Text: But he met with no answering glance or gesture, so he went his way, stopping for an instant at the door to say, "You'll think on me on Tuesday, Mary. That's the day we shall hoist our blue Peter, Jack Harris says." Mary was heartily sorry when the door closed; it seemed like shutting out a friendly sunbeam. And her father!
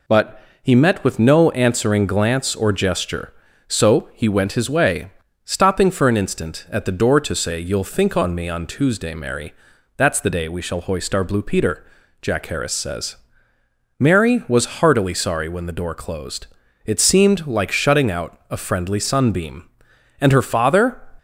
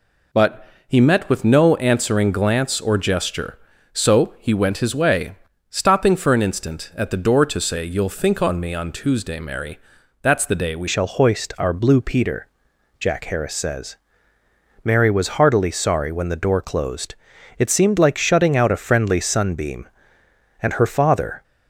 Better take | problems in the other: first | pauses between "But" and "he"; slight; at 0.6 s; 0.22 s long; slight in the first // changes voice at "shall"; from 10.8 s on; 10.6 s long

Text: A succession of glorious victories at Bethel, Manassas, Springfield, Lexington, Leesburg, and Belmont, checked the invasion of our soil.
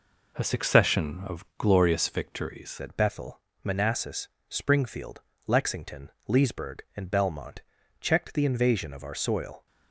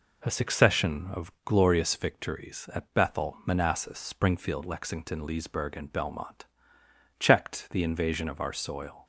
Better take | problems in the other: second | changes voice at "at"; from 2.7 s on; 6.9 s long

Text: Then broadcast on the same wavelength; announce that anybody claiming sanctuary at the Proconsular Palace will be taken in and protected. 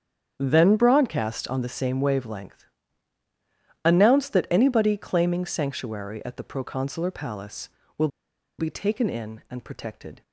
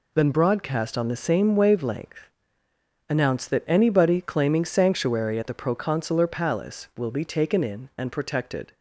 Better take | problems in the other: second | starts louder than the rest; strong; until 1.4 s; 8 dB // pauses between "will" and "be"; noticeable; at 8.0 s; 0.51 s long

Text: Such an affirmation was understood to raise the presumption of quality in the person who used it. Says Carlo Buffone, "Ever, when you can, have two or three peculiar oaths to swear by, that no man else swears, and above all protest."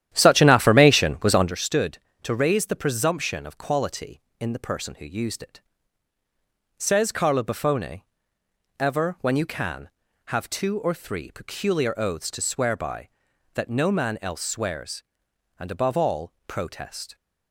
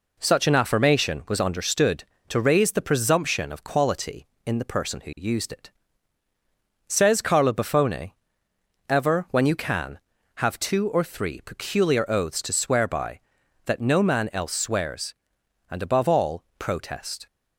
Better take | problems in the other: second | starts louder than the rest; strong; until 1.5 s; 11 dB

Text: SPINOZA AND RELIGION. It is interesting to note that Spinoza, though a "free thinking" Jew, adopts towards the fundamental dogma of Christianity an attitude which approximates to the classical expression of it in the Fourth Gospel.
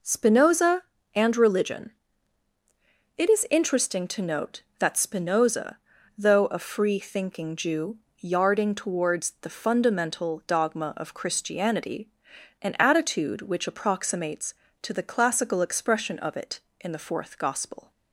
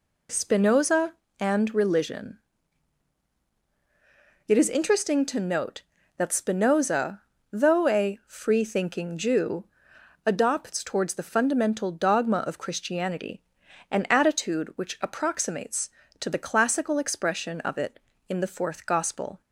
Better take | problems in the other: second | says "yarding" for "adopts"; at 8.1 s // pauses between "Christianity" and "an"; noticeable; at 12.0 s; 0.54 s long; noticeable in the second

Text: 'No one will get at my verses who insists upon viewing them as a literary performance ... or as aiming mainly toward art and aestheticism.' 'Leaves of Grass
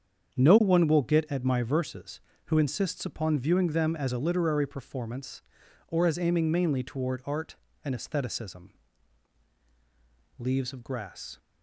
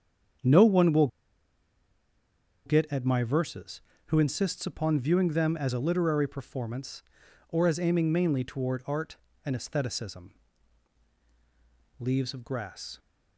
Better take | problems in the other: first | starts louder than the rest; strong; until 3.0 s; 7.5 dB; strong in the first // pauses between "will" and "get"; strong; at 1.0 s; 1.5 s long

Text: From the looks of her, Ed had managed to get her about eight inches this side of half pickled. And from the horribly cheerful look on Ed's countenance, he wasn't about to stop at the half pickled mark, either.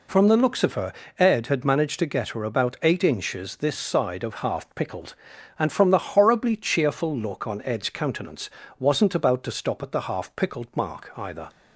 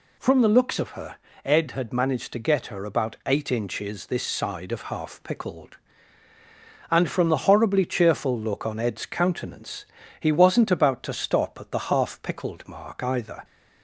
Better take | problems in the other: second | skips "he"; at 8.6 s

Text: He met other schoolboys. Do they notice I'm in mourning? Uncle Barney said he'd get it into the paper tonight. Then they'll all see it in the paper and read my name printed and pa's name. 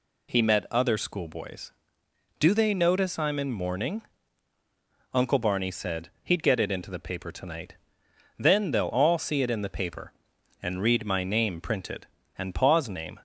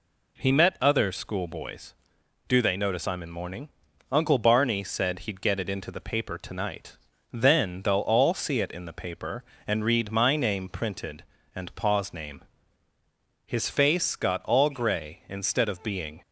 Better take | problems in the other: first | goes on to say "His face got all grey instead of being"; strong; from 13.4 s on; 2.7 s long

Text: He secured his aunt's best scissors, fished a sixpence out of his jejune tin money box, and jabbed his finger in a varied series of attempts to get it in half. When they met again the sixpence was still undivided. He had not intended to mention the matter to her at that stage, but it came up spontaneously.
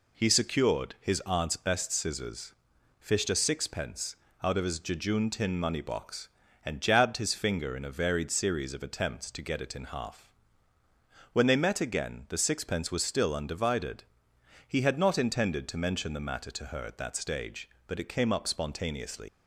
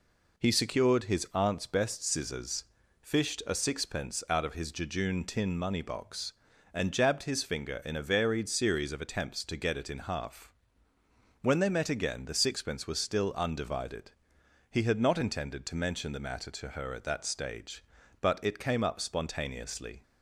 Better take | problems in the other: second | pauses between "sixpence" and "out"; slight; at 4.1 s; 0.30 s long // leaves "spontaneously" unfinished; at 19.2 s; 65 ms

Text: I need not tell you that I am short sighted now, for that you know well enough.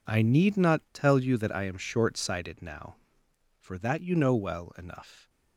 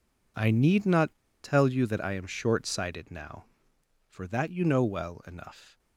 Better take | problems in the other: first | pauses between "not" and "tell"; slight; at 1.1 s; 0.26 s long

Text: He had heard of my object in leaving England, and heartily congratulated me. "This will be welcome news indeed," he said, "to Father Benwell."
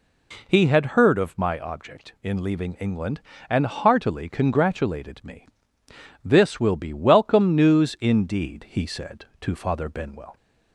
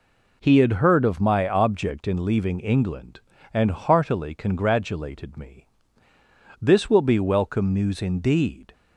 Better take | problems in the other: first | stops before "he said to Father Benwell"; at 8.7 s

